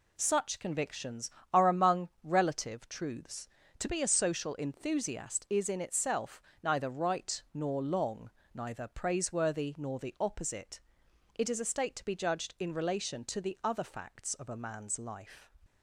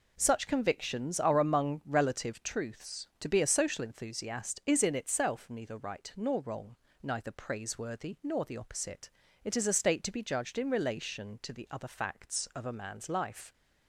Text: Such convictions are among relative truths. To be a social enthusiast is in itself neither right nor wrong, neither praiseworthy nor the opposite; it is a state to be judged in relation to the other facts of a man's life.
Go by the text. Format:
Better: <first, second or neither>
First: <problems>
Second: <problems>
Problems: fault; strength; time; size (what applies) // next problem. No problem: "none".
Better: second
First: pauses between "itself" and "neither"; slight; at 6.4 s; 0.22 s long // says "long" for "wrong"; at 7.8 s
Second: none